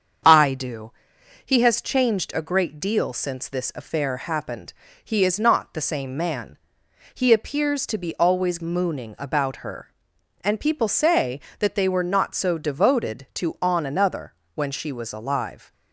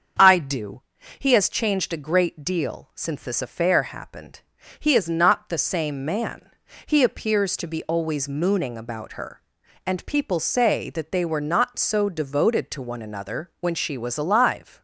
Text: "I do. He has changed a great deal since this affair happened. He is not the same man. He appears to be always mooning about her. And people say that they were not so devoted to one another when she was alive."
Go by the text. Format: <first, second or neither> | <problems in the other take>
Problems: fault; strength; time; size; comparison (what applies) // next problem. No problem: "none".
second | starts louder than the rest; strong; until 1.7 s; 7 dB; also in the second // says "on" for "one"; at 13.5 s // pauses between "another" and "when"; slight; at 14.3 s; 0.22 s long